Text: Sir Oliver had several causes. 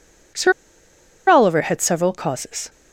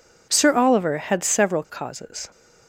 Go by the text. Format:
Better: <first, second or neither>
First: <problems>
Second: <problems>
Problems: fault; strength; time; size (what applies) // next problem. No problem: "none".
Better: second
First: pauses between "Sir" and "Oliver"; noticeable; at 0.5 s; 0.77 s long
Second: none